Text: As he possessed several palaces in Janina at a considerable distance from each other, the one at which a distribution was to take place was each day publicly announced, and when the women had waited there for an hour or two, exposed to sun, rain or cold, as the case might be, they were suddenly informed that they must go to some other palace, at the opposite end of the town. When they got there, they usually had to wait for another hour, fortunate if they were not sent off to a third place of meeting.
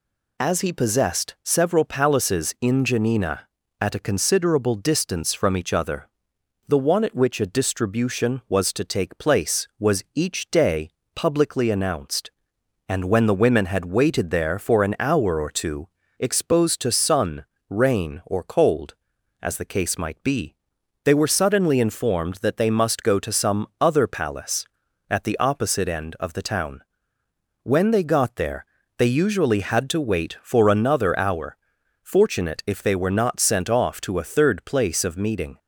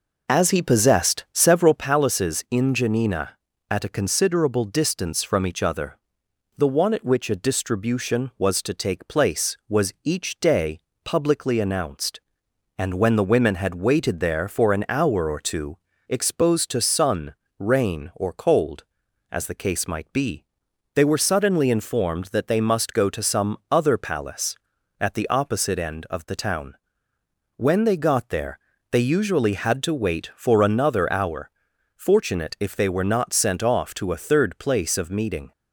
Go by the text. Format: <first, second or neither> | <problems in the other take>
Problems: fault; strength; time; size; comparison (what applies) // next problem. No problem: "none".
first | starts louder than the rest; noticeable; until 1.9 s; 5 dB // pauses between "day" and "publicly"; slight; at 10.8 s; 0.24 s long; slight in the first